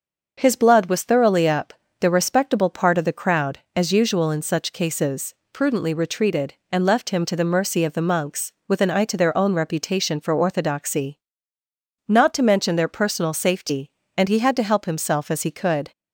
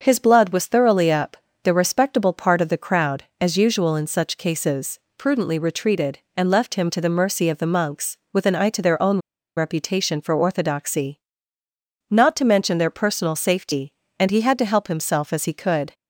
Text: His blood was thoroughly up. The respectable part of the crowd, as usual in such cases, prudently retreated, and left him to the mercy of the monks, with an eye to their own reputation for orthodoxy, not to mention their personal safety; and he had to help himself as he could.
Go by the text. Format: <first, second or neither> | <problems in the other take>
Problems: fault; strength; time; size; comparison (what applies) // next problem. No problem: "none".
first | starts louder than the rest; until 1.0 s; 6.5 dB; also in the first // pauses between "own" and "reputation"; at 9.1 s; 0.37 s long